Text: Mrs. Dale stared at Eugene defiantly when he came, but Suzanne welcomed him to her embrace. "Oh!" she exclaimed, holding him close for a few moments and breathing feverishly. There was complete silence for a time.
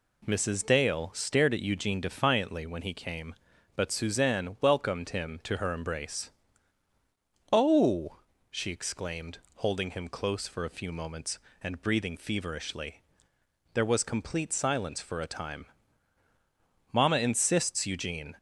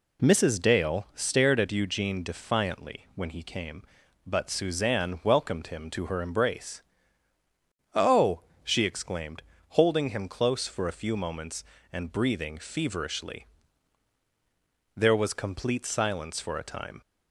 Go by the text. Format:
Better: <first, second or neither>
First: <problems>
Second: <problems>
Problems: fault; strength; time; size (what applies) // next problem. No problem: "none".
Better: second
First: goes on to say "Mama insists Eugene"; from 16.9 s on; 1.4 s long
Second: none